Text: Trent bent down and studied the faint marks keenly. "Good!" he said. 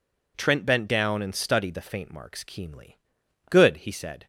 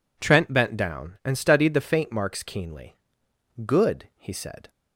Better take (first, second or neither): neither